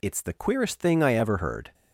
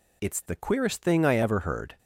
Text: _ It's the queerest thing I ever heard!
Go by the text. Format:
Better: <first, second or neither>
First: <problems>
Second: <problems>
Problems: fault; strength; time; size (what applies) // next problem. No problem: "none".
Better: neither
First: none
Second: none